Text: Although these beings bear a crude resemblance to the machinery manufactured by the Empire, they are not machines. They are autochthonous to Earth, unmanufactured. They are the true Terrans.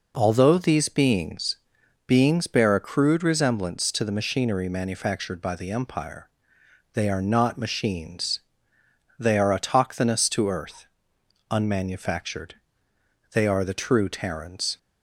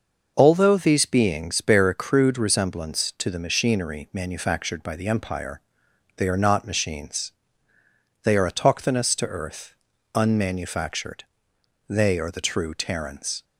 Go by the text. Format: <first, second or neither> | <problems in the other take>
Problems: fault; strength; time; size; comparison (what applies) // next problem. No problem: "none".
second | says "beings" twice; at 2.0 s